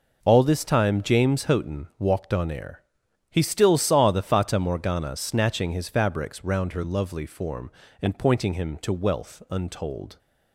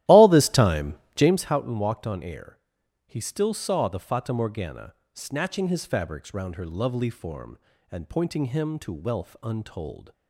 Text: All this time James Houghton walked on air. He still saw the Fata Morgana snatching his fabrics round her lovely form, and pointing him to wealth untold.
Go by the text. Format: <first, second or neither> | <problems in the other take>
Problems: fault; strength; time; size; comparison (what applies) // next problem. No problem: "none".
first | starts louder than the rest; strong; until 1.4 s; 14.5 dB // pauses between "time" and "James"; slight; at 0.9 s; 0.20 s long // pauses between "Morgana" and "snatching"; slight; at 4.9 s; 0.18 s long